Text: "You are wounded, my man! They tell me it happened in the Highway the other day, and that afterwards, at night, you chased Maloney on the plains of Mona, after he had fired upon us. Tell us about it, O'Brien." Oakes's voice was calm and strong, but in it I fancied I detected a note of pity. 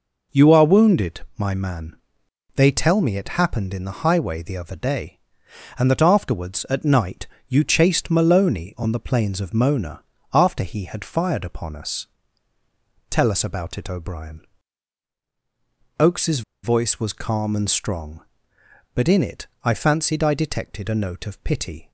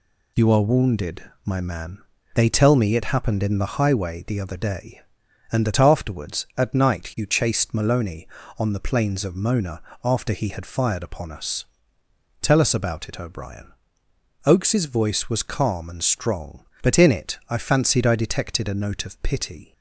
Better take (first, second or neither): second